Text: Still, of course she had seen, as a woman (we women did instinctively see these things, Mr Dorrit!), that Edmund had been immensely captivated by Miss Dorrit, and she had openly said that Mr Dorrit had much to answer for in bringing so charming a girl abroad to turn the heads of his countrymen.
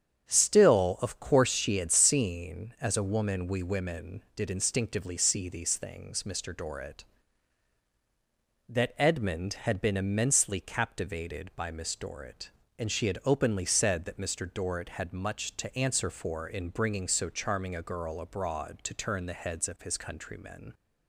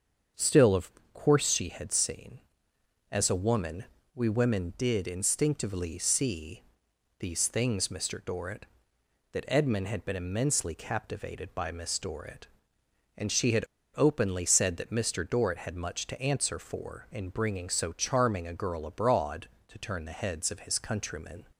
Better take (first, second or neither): first